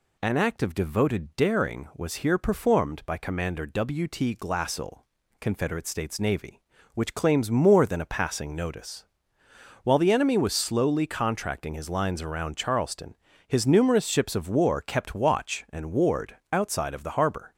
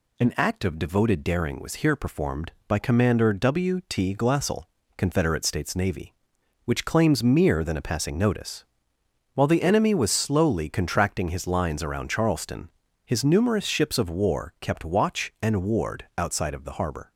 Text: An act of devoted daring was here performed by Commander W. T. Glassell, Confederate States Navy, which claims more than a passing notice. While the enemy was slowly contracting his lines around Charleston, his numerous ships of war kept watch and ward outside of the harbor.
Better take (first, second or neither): first